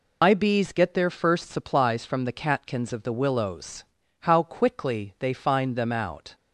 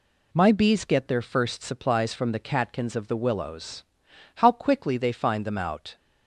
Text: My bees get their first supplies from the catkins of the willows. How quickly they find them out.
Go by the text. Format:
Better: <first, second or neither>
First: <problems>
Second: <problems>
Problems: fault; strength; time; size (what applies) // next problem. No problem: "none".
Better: second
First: loses the start of "My"; at 0.2 s; 110 ms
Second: none